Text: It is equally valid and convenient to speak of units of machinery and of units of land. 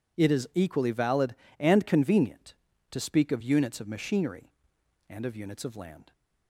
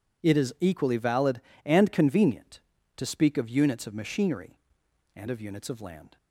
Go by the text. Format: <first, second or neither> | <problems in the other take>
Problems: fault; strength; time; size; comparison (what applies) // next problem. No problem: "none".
neither | none